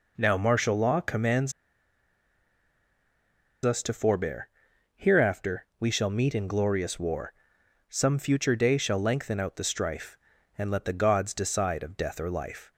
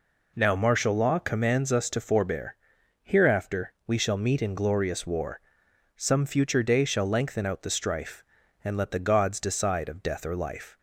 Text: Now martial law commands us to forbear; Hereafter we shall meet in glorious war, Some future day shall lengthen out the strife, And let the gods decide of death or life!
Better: second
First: pauses between "commands" and "us"; strong; at 1.5 s; 2.1 s long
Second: none

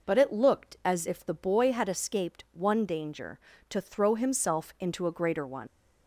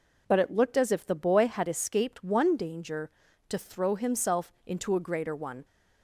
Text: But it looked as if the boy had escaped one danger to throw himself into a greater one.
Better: second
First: leaves "one" unfinished; at 5.6 s; 105 ms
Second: none

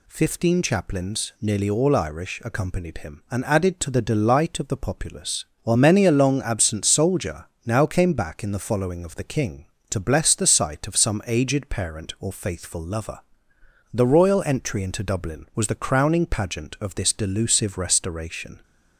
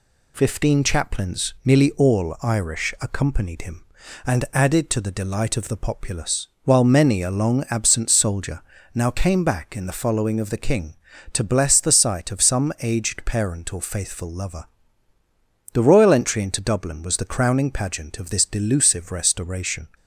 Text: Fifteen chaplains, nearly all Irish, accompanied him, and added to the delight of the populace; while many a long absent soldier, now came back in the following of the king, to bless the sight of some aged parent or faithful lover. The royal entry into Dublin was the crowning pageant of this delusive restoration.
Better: neither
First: none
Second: none

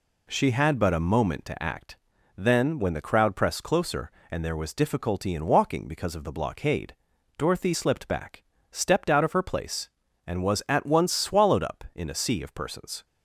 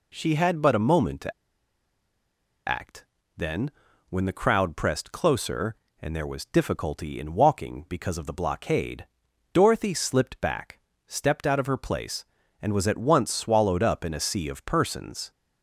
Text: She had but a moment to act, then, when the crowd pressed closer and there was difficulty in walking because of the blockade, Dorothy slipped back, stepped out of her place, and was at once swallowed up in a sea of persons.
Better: first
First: none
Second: pauses between "to" and "act"; strong; at 1.3 s; 1.3 s long

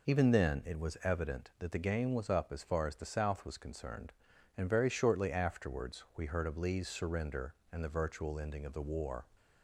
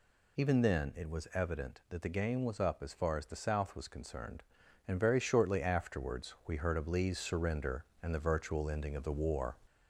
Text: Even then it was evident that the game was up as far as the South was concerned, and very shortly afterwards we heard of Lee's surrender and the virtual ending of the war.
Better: first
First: none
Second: gets louder; slight; throughout; 2.5 dB

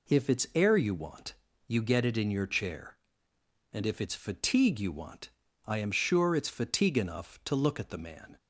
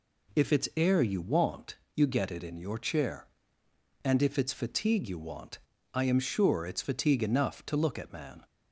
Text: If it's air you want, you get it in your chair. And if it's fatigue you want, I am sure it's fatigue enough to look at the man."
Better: first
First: none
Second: skips "the"; at 8.1 s

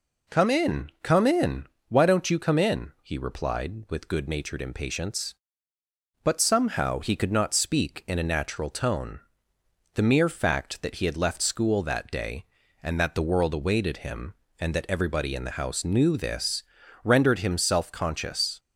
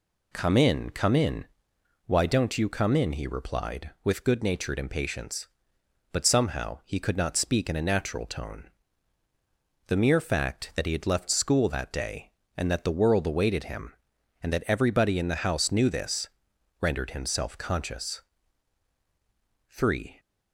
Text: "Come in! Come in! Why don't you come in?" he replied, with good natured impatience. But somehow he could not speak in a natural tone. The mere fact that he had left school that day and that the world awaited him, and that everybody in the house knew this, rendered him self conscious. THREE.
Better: second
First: stops before "THREE"; at 18.5 s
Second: none

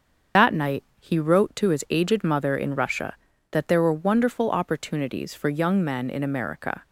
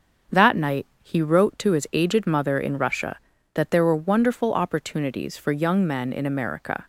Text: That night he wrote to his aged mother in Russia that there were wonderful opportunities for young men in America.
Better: second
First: loses the start of "That"; at 0.3 s; 85 ms // starts louder than the rest; until 1.5 s; 7 dB // pauses between "night" and "he"; slight; at 0.8 s; 0.16 s long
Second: starts louder than the rest; until 1.4 s; 7 dB // pauses between "night" and "he"; slight; at 0.8 s; 0.16 s long

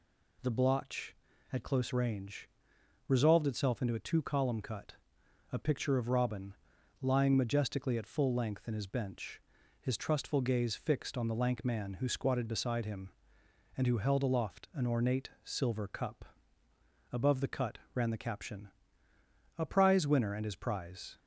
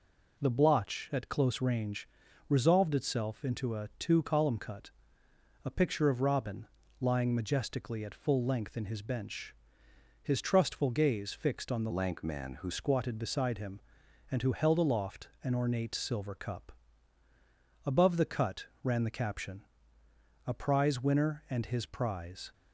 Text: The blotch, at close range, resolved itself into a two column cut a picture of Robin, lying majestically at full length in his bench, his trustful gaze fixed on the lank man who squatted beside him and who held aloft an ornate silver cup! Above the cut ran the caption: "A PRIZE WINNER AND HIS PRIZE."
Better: first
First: pauses between "cut" and "a"; noticeable; at 4.9 s; 0.58 s long // pauses between "cut" and "ran"; slight; at 17.7 s; 0.16 s long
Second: pauses between "cut" and "a"; noticeable; at 4.8 s; 0.74 s long // changes voice from "lank" to "who"; from 11.9 to 12.6 s; 0.7 s long // pauses between "cut" and "ran"; slight; at 18.6 s; 0.16 s long

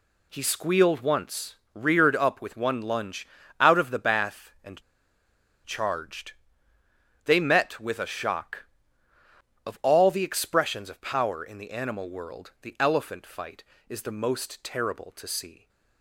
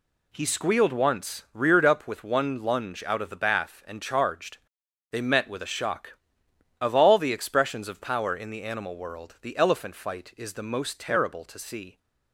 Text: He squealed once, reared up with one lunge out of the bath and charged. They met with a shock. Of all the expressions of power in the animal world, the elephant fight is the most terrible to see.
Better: second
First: pauses between "lunge" and "out"; slight; at 3.2 s; 0.34 s long // pauses between "and" and "charged"; noticeable; at 4.8 s; 0.84 s long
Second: none

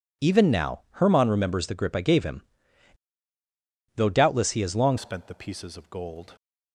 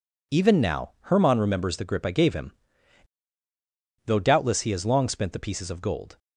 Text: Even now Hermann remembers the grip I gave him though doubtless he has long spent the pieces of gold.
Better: second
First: pauses between "him" and "though"; strong; at 2.4 s; 1.5 s long // changes voice at "spent"; from 4.9 s on; 1.4 s long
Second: pauses between "him" and "though"; strong; at 2.5 s; 1.5 s long

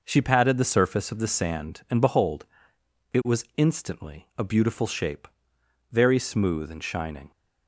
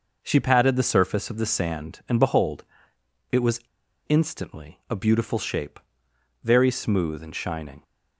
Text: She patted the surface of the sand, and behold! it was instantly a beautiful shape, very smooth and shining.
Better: first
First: none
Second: pauses between "was" and "instantly"; noticeable; at 3.6 s; 0.48 s long

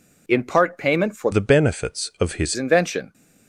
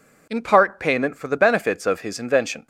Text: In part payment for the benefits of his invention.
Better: second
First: changes voice from "the" to "his"; from 1.3 to 2.5 s; 1.2 s long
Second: none

